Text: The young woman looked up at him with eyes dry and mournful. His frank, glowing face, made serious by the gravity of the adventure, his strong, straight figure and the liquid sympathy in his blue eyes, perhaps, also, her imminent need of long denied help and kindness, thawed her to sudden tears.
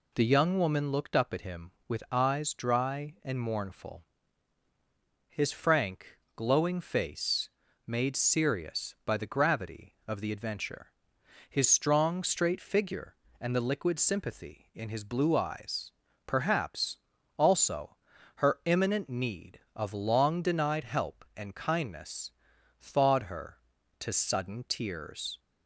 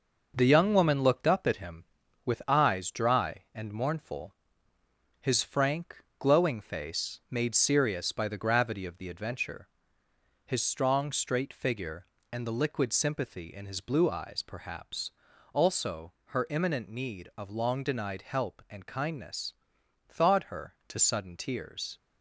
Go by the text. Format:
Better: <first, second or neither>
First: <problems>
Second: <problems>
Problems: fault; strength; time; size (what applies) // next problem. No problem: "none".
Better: first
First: none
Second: gets quieter; noticeable; throughout; 5 dB